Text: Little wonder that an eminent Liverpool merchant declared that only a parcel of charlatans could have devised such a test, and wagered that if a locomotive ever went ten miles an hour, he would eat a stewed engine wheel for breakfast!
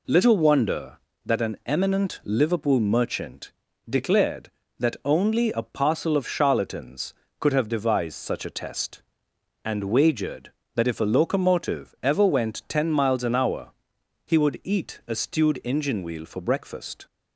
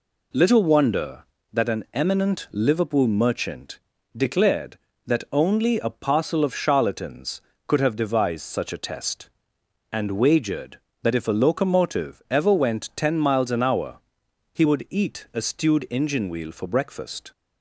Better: neither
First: pauses between "merchant" and "declared"; slight; at 3.5 s; 0.36 s long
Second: pauses between "merchant" and "declared"; slight; at 3.7 s; 0.36 s long

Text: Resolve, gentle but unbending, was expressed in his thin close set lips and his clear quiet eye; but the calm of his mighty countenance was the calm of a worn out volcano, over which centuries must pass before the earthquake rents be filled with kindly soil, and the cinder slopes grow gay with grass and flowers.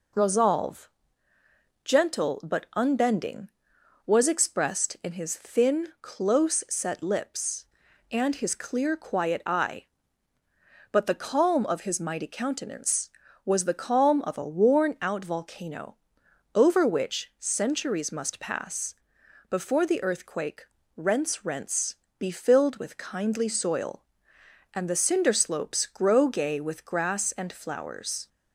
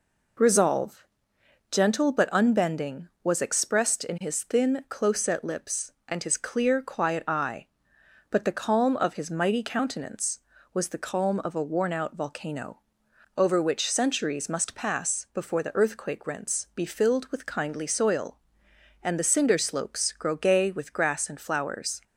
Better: second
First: pauses between "pass" and "before"; noticeable; at 18.9 s; 0.56 s long // pauses between "earthquake" and "rents"; slight; at 20.6 s; 0.28 s long // says "rents" twice; at 21.4 s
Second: none

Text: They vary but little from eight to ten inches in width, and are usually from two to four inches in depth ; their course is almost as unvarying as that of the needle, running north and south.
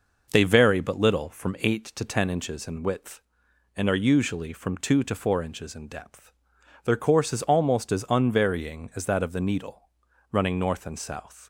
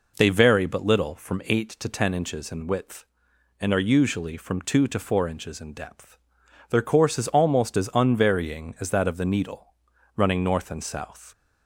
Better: second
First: gets quieter; throughout; 4 dB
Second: none

